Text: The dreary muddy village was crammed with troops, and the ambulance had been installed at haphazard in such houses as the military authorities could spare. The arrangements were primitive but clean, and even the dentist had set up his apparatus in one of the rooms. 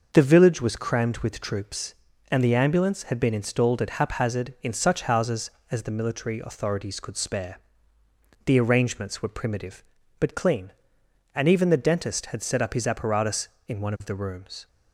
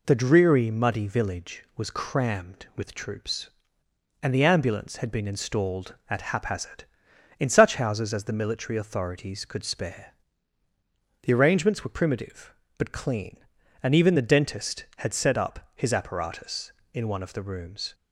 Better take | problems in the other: second | skips "dreary muddy"; at 0.2 s

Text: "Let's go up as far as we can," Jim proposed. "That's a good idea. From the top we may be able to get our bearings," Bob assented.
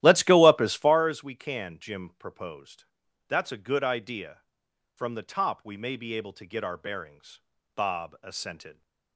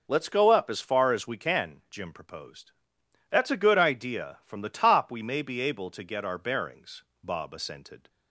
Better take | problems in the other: second | starts louder than the rest; strong; until 1.1 s; 13.5 dB

